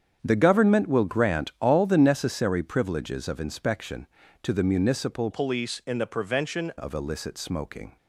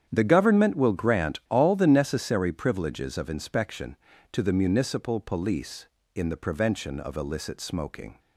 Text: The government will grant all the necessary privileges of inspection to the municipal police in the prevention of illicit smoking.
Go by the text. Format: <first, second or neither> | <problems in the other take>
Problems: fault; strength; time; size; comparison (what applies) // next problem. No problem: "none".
second | starts louder than the rest; strong; until 1.2 s; 8 dB; strong in the second // changes voice from "police" to "prevention"; from 5.3 to 6.7 s; 1.4 s long